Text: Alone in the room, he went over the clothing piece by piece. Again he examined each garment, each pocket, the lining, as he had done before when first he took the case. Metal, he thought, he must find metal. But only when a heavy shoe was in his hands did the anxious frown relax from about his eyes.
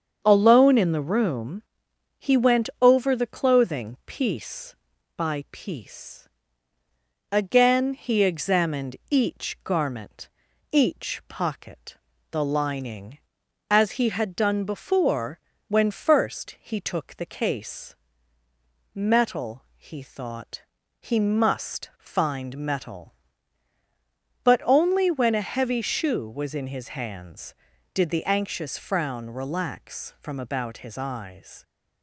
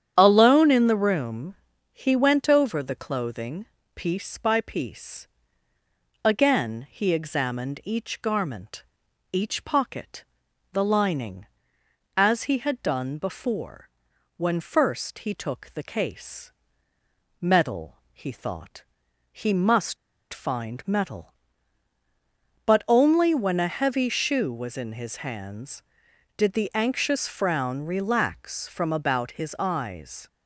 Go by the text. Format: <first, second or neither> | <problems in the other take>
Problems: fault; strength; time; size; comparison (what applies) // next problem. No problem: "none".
first | starts louder than the rest; strong; until 1.1 s; 9 dB; strong in the first // pauses between "clothing" and "piece"; slight; at 3.6 s; 0.32 s long // pauses between "before" and "when"; noticeable; at 13.8 s; 0.48 s long; slight in the first // pauses between "must" and "find"; at 19.9 s; 0.36 s long